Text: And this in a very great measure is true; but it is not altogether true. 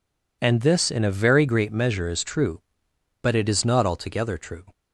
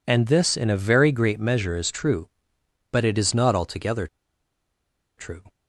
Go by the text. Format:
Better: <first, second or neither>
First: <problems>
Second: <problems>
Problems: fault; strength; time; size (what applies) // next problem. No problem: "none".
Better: first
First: none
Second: pauses between "altogether" and "true"; at 4.0 s; 1.1 s long